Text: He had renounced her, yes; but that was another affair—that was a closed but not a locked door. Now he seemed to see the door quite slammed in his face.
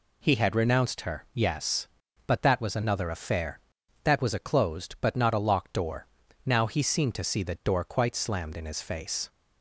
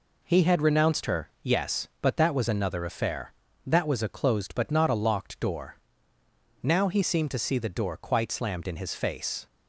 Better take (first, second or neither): neither